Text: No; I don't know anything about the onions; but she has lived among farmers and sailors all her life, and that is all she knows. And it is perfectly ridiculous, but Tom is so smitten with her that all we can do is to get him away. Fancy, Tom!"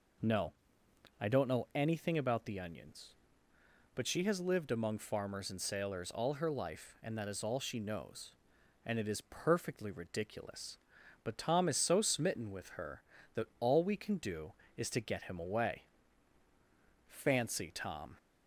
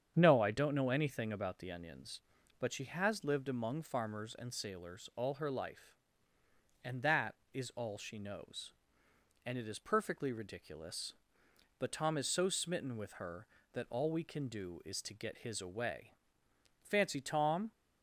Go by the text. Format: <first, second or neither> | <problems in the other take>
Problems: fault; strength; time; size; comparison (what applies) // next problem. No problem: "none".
first | starts louder than the rest; strong; until 1.1 s; 8 dB // says "his" for "him"; at 15.3 s